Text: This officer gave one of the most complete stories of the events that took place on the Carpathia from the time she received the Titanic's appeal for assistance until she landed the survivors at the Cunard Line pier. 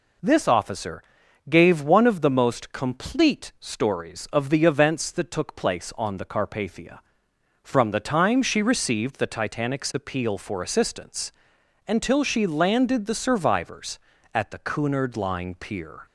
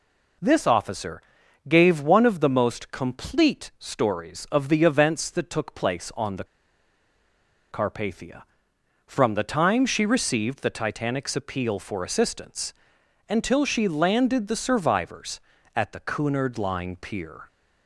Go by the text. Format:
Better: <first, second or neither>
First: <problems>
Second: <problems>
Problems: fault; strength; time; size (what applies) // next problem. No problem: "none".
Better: first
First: pauses between "officer" and "gave"; at 1.0 s; 0.44 s long // pauses between "assistance" and "until"; noticeable; at 11.3 s; 0.56 s long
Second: pauses between "officer" and "gave"; at 1.2 s; 0.44 s long // pauses between "the" and "Carpathia"; strong; at 6.4 s; 1.2 s long // pauses between "assistance" and "until"; noticeable; at 12.7 s; 0.56 s long